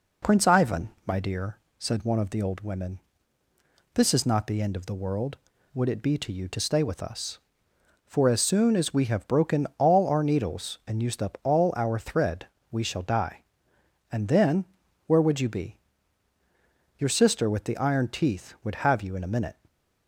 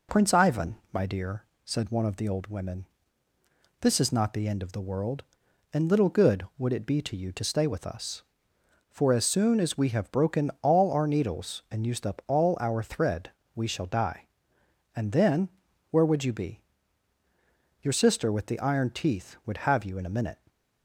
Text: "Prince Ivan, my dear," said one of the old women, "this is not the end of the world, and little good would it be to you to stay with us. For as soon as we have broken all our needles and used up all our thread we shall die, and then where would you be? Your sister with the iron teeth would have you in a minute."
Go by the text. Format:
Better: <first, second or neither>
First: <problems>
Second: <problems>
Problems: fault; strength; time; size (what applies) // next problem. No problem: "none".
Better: second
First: skips "and little good"; at 5.5 s // pauses between "thread" and "we"; slight; at 12.4 s; 0.24 s long // pauses between "then" and "where"; at 14.6 s; 0.44 s long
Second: pauses between "thread" and "we"; slight; at 13.2 s; 0.24 s long // pauses between "then" and "where"; at 15.4 s; 0.44 s long